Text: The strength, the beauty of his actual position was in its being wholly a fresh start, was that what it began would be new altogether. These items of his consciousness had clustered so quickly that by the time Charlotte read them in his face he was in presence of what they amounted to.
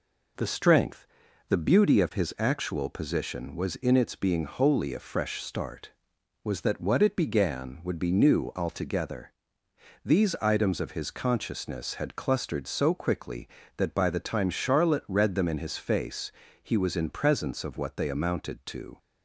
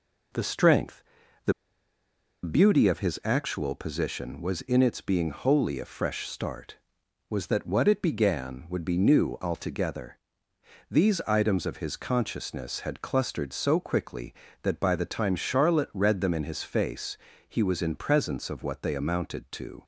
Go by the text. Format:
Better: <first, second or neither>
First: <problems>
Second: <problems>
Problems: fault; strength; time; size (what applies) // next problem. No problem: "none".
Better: first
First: pauses between "face" and "he"; slight; at 16.2 s; 0.32 s long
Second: pauses between "the" and "beauty"; noticeable; at 1.5 s; 0.91 s long // pauses between "face" and "he"; slight; at 17.1 s; 0.32 s long